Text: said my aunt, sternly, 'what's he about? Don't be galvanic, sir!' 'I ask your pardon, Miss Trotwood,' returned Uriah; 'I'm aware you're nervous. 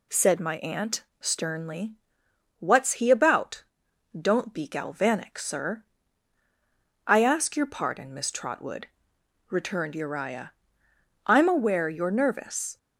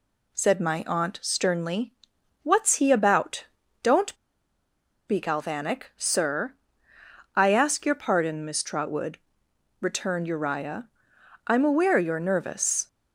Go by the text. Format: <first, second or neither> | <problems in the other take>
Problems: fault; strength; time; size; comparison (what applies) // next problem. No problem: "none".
first | pauses between "Don't" and "be"; noticeable; at 4.1 s; 0.93 s long